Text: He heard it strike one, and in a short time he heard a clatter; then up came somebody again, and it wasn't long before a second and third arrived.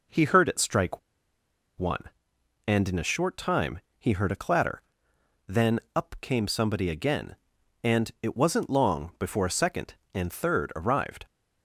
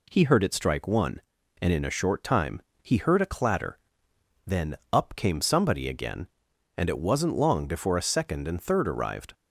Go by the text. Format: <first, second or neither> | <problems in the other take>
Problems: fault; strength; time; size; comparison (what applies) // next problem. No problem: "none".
second | pauses between "strike" and "one"; noticeable; at 0.9 s; 0.79 s long // pauses between "time" and "he"; slight; at 3.7 s; 0.20 s long; slight in the second // pauses between "then" and "up"; slight; at 5.8 s; 0.16 s long; slight in the second